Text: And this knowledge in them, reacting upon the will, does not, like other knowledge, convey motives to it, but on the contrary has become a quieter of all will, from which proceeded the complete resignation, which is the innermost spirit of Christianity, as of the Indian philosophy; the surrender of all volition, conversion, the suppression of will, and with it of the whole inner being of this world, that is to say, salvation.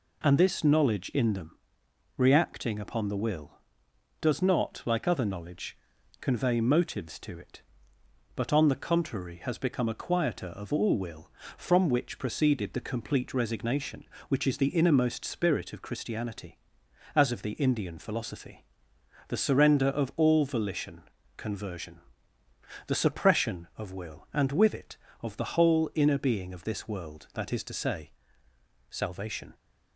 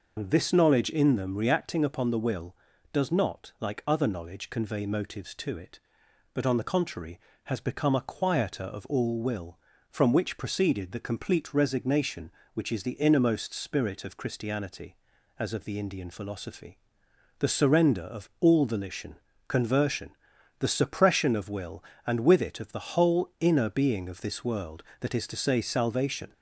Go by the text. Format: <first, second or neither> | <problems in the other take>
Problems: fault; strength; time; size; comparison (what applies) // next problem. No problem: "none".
first | loses the start of "And"; at 0.1 s; 105 ms